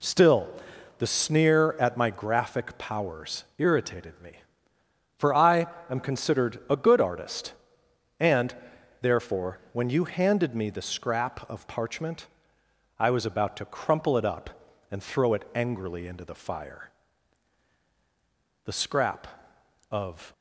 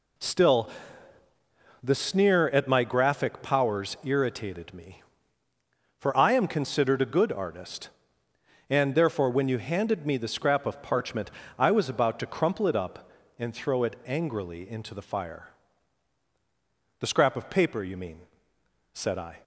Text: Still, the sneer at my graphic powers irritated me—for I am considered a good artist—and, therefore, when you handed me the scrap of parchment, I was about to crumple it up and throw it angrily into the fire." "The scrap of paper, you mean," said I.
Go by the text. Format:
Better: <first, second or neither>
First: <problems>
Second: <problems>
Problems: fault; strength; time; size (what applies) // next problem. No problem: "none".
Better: second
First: pauses between "powers" and "irritated"; slight; at 3.4 s; 0.16 s long // pauses between "I" and "am"; slight; at 5.6 s; 0.24 s long // stops before "paper you mean said I"; at 20.3 s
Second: none